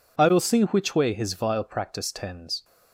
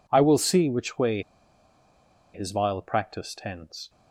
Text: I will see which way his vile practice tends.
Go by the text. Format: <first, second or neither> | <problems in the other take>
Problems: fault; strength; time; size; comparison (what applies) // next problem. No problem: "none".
first | pauses between "way" and "his"; at 1.2 s; 1.1 s long